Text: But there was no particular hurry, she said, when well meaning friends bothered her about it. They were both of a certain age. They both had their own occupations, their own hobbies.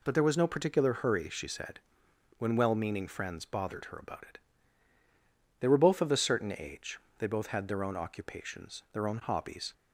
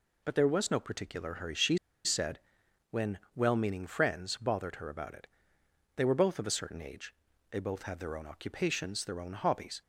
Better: first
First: none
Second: pauses between "she" and "said"; slight; at 1.7 s; 0.27 s long // pauses between "when" and "well"; slight; at 3.1 s; 0.16 s long

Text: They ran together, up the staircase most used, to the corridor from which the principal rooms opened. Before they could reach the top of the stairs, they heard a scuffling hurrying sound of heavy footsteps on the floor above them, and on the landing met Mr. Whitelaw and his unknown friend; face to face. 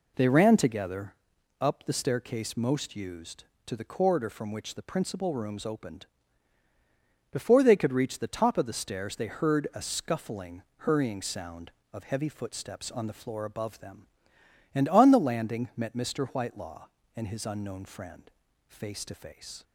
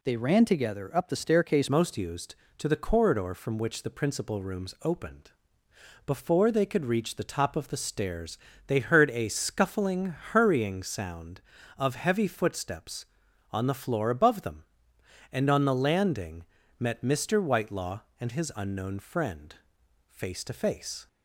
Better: first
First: pauses between "scuffling" and "hurrying"; slight; at 10.6 s; 0.16 s long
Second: changes voice at "most"; from 1.6 s on; 19.4 s long // pauses between "scuffling" and "hurrying"; slight; at 10.1 s; 0.16 s long // pauses between "landing" and "met"; slight; at 16.4 s; 0.36 s long

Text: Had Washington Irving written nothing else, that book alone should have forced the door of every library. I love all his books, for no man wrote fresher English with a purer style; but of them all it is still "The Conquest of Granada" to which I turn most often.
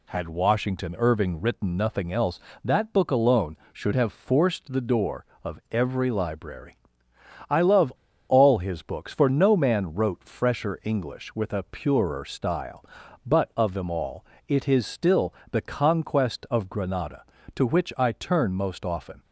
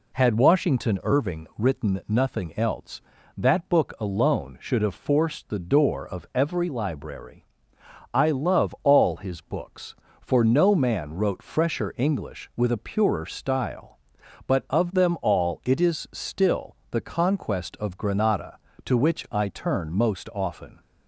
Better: second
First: pauses between "love" and "all"; at 7.9 s; 0.36 s long // pauses between "all" and "it"; slight; at 14.2 s; 0.24 s long // pauses between "still" and "The"; slight; at 15.3 s; 0.16 s long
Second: none

